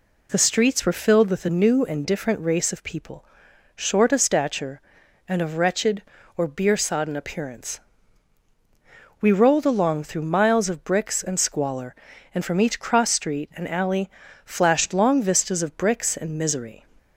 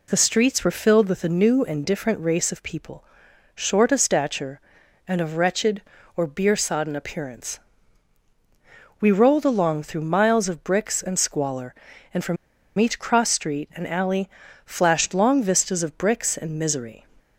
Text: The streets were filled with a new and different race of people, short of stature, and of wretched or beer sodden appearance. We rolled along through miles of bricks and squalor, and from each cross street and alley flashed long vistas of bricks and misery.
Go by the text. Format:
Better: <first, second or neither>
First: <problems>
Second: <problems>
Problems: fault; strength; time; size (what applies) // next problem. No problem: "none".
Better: first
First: pauses between "alley" and "flashed"; at 14.0 s; 0.37 s long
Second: pauses between "from" and "each"; at 12.3 s; 0.42 s long // pauses between "alley" and "flashed"; at 14.2 s; 0.38 s long